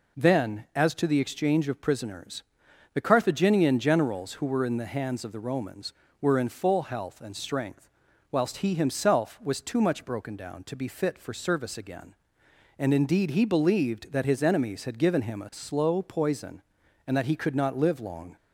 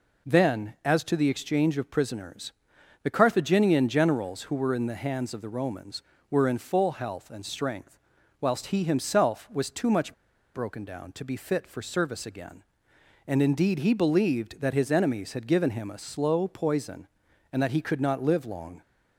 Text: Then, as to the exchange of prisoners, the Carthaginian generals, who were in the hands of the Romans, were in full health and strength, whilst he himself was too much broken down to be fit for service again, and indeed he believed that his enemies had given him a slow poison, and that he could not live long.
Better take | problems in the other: first | pauses between "much" and "broken"; at 10.1 s; 0.40 s long

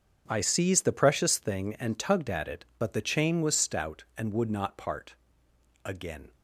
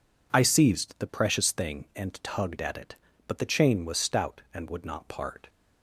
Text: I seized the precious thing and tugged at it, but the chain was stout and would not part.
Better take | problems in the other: second | starts louder than the rest; strong; until 1.3 s; 7 dB // goes on to say "Again"; from 5.8 s on; 0.50 s long

